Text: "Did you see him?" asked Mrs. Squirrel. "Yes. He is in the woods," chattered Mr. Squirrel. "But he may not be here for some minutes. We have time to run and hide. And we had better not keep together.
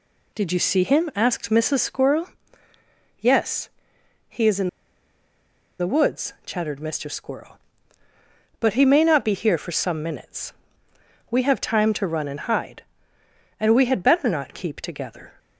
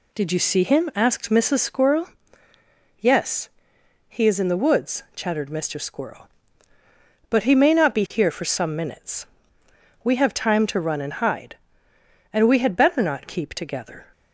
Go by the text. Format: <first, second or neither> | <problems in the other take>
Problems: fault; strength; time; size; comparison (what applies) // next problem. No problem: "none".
second | pauses between "in" and "the"; at 4.6 s; 1.1 s long